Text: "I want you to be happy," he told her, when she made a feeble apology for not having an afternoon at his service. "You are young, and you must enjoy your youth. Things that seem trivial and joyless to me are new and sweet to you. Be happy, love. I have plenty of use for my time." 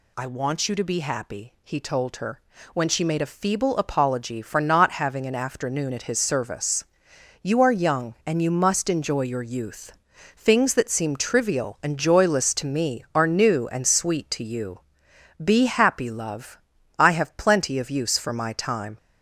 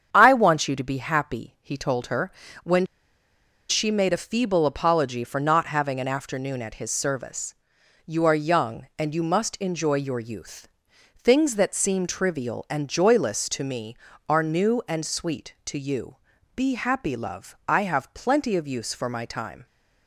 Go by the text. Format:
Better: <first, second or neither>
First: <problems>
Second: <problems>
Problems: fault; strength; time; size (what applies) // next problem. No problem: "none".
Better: first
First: none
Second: starts louder than the rest; strong; until 1.1 s; 8 dB // pauses between "when" and "she"; noticeable; at 2.8 s; 0.84 s long